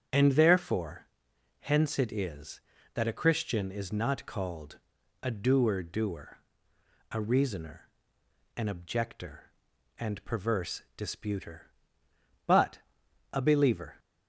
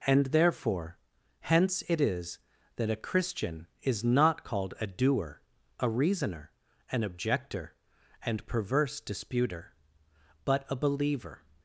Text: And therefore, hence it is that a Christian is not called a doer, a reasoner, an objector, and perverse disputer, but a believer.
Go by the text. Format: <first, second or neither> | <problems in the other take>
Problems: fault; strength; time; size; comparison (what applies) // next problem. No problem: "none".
second | starts louder than the rest; strong; until 1.6 s; 8 dB // pauses between "called" and "a"; at 4.7 s; 0.44 s long // says "doer" twice; at 5.8 s // pauses between "but" and "a"; noticeable; at 12.7 s; 0.54 s long